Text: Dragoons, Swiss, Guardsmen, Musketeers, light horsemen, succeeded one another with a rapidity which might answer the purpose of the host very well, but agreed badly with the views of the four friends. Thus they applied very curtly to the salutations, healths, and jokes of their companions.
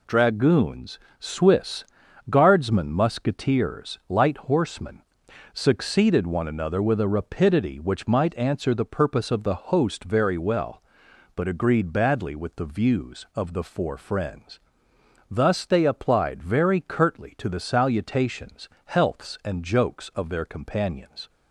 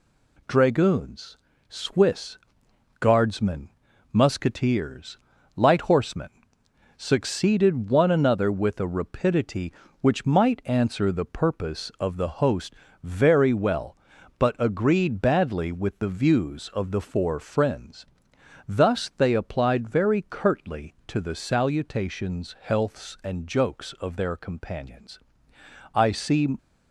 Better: first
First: none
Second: pauses between "host" and "very"; slight; at 12.7 s; 0.28 s long // goes on to say "I see"; noticeable; from 25.9 s on; 0.62 s long

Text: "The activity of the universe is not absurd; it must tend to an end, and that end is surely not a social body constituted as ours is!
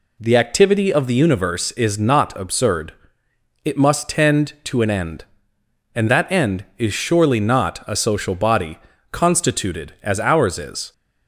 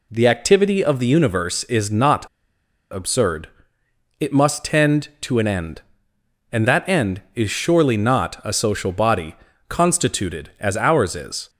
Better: first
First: pauses between "body" and "constituted"; slight; at 8.7 s; 0.34 s long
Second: pauses between "not" and "absurd"; noticeable; at 2.2 s; 0.67 s long // pauses between "body" and "constituted"; slight; at 9.3 s; 0.34 s long

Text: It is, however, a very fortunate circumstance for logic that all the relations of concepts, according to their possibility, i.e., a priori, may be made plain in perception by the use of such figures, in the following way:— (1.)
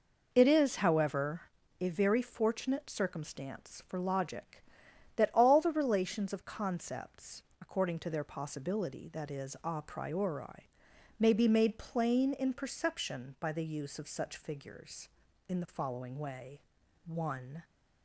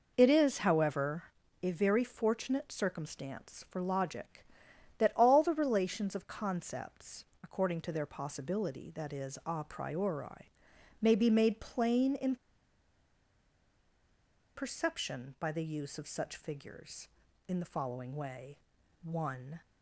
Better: first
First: none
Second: pauses between "in" and "perception"; strong; at 12.3 s; 2.2 s long

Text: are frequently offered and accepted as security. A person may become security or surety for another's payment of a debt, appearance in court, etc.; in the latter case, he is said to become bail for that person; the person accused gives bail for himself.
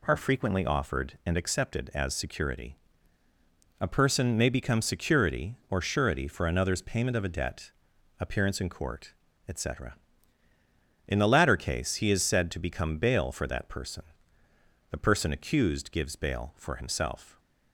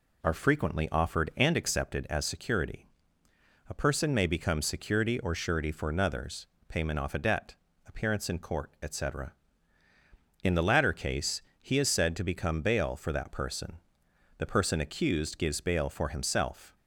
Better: first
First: none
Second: pauses between "another's" and "payment"; slight; at 6.4 s; 0.20 s long // says "off" for "of"; at 6.9 s

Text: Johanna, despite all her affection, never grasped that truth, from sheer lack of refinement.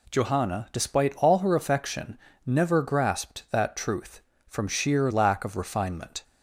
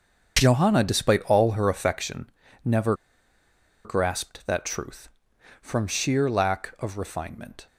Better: first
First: none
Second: starts louder than the rest; until 1.4 s; 7 dB // pauses between "never" and "grasped"; noticeable; at 2.9 s; 0.91 s long

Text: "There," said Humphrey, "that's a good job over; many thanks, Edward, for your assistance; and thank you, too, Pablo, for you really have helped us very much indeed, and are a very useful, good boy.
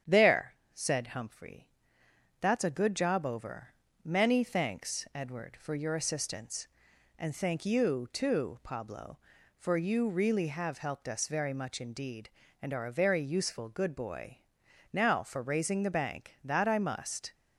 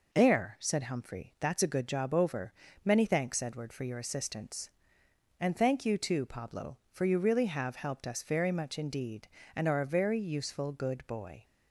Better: second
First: starts louder than the rest; strong; until 1.2 s; 8.5 dB // goes on to say "Now for raising the bank that I must"; strong; from 14.9 s on; 2.4 s long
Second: none

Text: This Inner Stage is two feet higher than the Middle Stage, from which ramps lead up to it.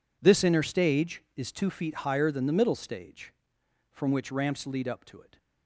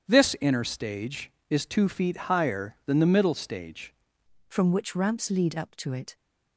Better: first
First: none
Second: starts louder than the rest; strong; until 1.1 s; 8 dB // changes voice at "from"; from 4.4 s on; 1.7 s long

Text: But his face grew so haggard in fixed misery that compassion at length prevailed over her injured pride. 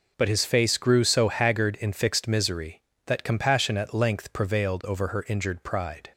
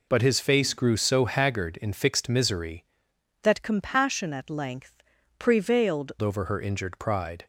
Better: first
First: none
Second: changes voice from "that" to "prevailed"; from 3.4 to 6.1 s; 2.7 s long // pauses between "length" and "prevailed"; slight; at 5.0 s; 0.36 s long

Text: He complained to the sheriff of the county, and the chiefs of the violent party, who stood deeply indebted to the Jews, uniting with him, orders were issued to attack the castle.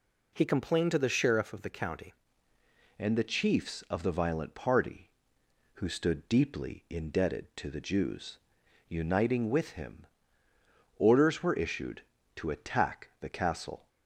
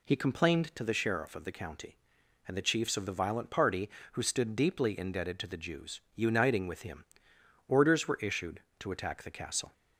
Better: second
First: changes voice at "and"; from 2.9 s on; 10.9 s long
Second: none

